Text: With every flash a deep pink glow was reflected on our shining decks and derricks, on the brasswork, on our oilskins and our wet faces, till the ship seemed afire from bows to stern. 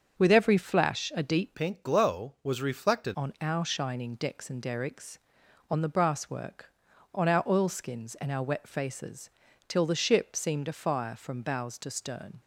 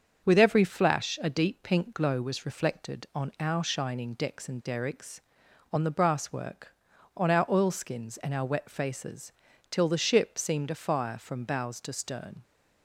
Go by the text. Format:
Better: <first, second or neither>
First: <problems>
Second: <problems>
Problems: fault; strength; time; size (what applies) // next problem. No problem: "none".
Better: second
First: starts louder than the rest; until 1.2 s; 7 dB // changes voice from "pink" to "reflected"; from 1.5 to 3.1 s; 1.6 s long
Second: starts louder than the rest; until 1.2 s; 6.5 dB